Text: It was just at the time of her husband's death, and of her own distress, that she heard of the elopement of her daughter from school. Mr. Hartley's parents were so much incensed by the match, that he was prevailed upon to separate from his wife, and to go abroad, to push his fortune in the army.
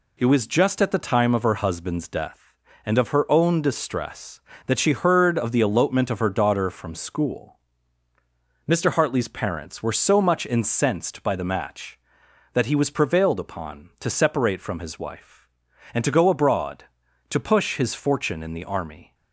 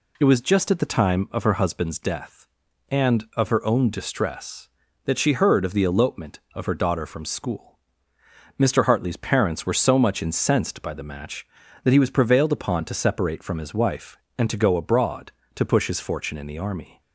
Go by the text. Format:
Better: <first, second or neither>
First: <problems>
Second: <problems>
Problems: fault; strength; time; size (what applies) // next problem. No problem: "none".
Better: neither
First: none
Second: none